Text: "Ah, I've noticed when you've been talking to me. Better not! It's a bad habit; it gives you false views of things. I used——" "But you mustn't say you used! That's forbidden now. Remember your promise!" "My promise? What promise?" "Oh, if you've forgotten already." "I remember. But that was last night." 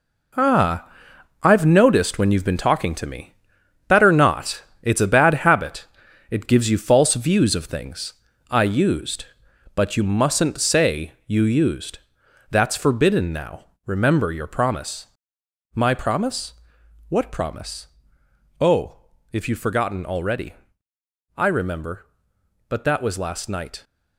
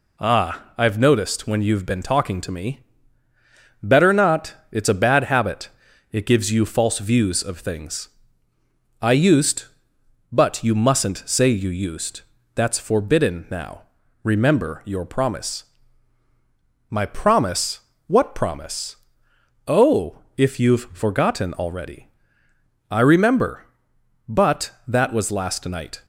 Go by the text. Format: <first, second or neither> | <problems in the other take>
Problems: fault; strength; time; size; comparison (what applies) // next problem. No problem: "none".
second | gets quieter; strong; throughout; 9 dB // pauses between "say" and "you"; slight; at 11.1 s; 0.16 s long